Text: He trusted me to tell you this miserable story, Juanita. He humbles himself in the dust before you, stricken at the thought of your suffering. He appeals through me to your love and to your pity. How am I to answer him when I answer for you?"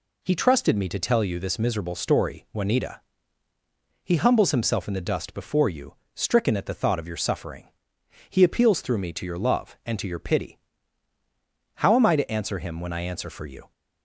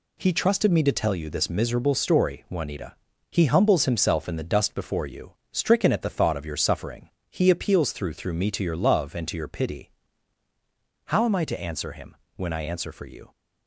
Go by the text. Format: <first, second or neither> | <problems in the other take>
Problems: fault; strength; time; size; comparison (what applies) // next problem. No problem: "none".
first | says "through" twice; at 8.1 s // pauses between "him" and "when"; slight; at 12.1 s; 0.18 s long